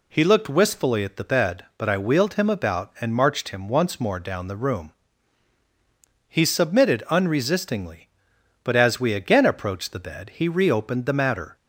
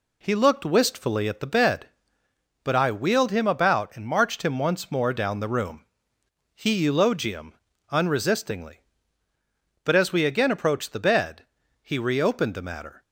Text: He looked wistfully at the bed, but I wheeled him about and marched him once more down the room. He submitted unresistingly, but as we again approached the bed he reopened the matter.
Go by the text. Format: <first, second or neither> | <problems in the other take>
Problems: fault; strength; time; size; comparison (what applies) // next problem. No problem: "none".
first | says "eulogium" for "submitted"; at 6.8 s // pauses between "bed" and "he"; at 11.4 s; 0.38 s long